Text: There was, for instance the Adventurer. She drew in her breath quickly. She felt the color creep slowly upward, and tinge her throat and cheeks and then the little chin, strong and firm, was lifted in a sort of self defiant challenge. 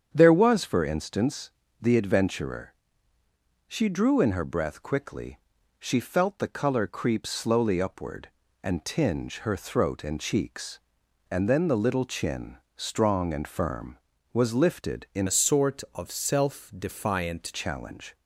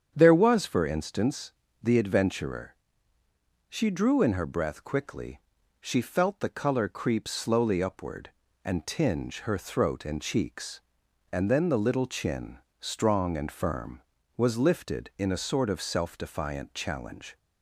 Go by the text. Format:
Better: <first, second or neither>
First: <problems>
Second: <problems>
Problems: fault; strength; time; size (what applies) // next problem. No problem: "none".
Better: second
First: starts louder than the rest; strong; until 1.1 s; 8 dB // pauses between "instance" and "the"; slight; at 1.5 s; 0.32 s long // changes voice from "a" to "defiant"; from 15.2 to 17.5 s; 2.3 s long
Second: starts louder than the rest; strong; until 1.1 s; 8 dB // pauses between "instance" and "the"; slight; at 1.5 s; 0.32 s long